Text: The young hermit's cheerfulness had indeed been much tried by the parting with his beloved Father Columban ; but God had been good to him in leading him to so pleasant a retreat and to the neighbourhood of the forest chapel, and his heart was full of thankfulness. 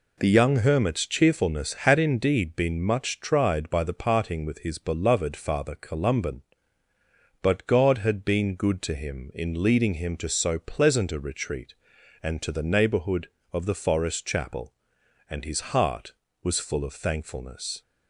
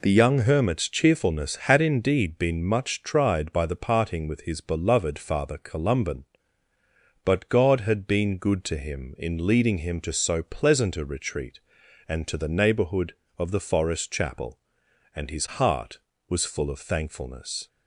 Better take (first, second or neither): neither